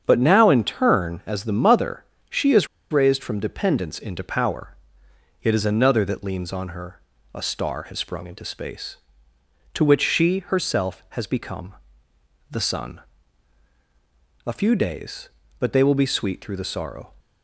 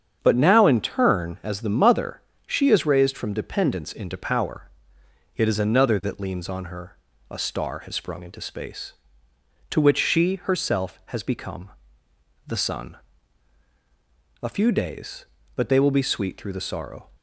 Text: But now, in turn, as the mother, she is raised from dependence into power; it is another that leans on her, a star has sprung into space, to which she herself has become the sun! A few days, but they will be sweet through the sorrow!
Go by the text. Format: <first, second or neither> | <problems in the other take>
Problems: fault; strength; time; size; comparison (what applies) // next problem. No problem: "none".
second | starts louder than the rest; strong; until 1.0 s; 7.5 dB; strong in the second // pauses between "is" and "raised"; slight; at 2.6 s; 0.24 s long // pauses between "become" and "the"; noticeable; at 11.7 s; 0.76 s long; noticeable in the second